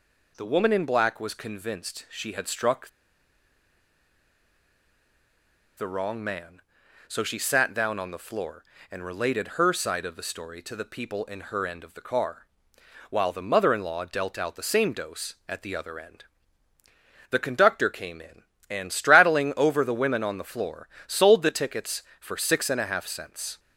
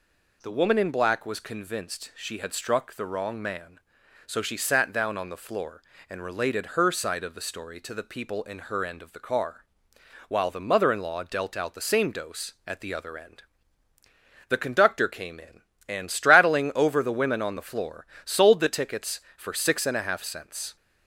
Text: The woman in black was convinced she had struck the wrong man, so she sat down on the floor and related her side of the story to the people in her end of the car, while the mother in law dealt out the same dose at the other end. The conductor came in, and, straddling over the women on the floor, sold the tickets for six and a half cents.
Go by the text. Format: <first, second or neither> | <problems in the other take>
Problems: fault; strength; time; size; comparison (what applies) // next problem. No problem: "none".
second | pauses between "struck" and "the"; strong; at 2.8 s; 2.8 s long